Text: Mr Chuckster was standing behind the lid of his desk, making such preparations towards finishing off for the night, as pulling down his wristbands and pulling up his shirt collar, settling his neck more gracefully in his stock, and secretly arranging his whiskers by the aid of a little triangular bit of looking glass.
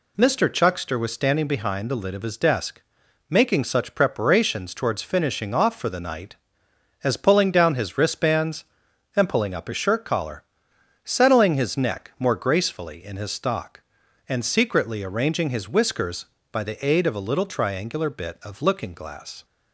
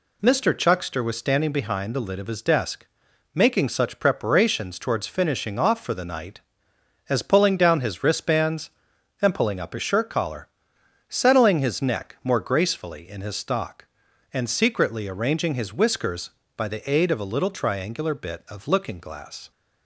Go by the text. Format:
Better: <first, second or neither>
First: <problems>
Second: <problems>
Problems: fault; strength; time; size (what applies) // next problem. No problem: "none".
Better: neither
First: none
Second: none